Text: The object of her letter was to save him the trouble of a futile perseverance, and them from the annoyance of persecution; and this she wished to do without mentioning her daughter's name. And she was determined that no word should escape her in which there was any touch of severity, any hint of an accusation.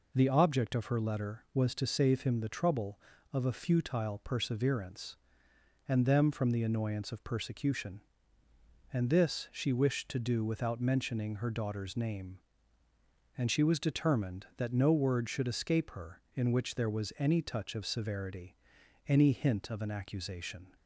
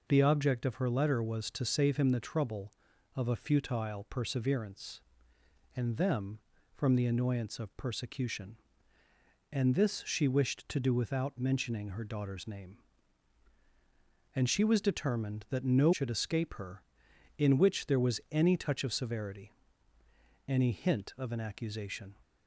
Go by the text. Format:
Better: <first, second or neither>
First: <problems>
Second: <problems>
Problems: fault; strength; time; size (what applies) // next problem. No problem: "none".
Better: first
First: none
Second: skips "word"; at 15.9 s